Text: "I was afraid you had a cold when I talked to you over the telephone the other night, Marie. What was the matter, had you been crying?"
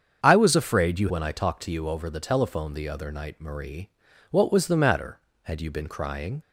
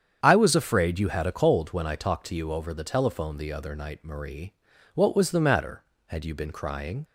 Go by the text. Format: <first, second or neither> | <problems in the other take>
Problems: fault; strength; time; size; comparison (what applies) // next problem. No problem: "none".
second | starts louder than the rest; strong; until 1.2 s; 7 dB; strong in the second // skips "had a cold"; at 1.0 s